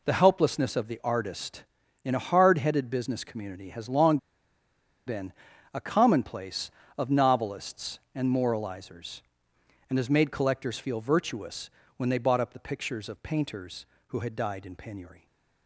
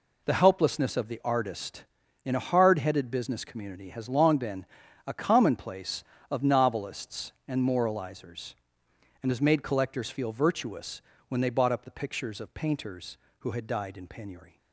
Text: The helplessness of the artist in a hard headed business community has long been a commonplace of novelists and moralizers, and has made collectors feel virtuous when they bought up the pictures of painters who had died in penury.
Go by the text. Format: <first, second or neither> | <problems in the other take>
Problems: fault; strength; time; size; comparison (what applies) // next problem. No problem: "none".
second | pauses between "long" and "been"; noticeable; at 4.1 s; 0.90 s long // pauses between "been" and "a"; at 5.3 s; 0.40 s long; also in the second // pauses between "virtuous" and "when"; slight; at 11.6 s; 0.28 s long; slight in the second